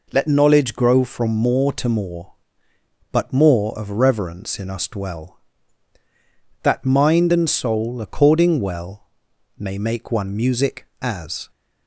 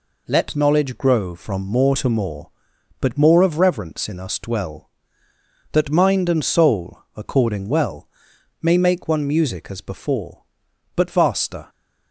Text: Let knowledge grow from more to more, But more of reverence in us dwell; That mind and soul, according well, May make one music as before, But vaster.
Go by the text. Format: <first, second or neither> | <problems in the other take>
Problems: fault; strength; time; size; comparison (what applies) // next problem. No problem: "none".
second | stops before "before But vaster"; at 11.5 s